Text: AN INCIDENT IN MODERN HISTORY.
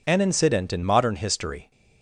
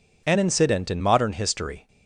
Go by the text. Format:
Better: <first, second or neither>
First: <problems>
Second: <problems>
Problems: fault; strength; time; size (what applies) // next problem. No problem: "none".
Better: neither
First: none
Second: none